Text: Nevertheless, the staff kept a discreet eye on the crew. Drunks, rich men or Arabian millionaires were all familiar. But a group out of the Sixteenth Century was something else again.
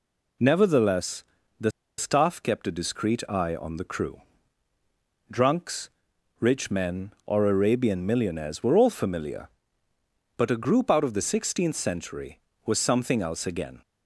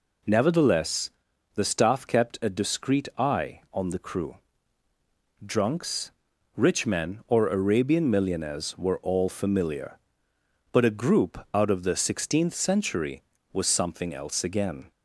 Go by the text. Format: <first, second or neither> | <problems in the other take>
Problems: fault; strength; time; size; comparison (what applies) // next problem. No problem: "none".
second | pauses between "the" and "staff"; slight; at 1.7 s; 0.28 s long